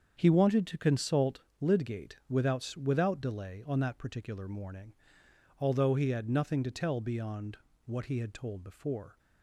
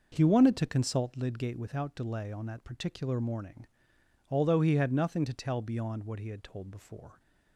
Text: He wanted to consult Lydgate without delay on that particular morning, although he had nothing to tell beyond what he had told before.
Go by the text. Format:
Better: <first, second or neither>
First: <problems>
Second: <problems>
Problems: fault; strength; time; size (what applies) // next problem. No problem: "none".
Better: second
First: starts louder than the rest; strong; until 1.1 s; 7 dB // pauses between "consult" and "Lydgate"; slight; at 1.4 s; 0.18 s long // says "without" twice; at 2.7 s // pauses between "beyond" and "what"; slight; at 7.5 s; 0.30 s long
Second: none